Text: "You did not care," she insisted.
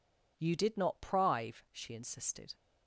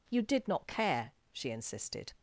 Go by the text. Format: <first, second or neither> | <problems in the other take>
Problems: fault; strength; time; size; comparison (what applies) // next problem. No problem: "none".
second | says "prive" for "care"; at 1.0 s